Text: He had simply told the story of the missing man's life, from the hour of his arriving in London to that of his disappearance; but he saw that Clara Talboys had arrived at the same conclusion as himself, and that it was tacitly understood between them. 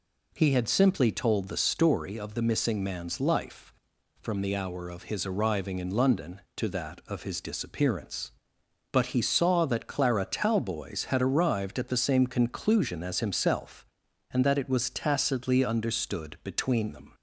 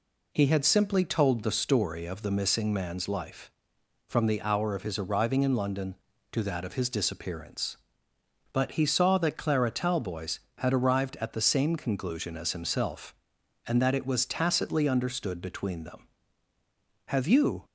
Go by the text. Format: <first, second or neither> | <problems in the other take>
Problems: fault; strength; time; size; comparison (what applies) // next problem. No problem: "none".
first | goes on to say "Have you"; from 17.0 s on; 0.56 s long